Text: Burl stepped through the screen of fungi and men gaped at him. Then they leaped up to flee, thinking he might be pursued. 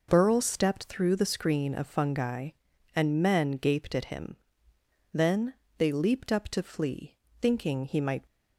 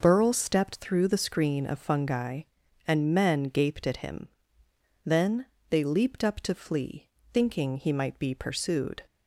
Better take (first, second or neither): second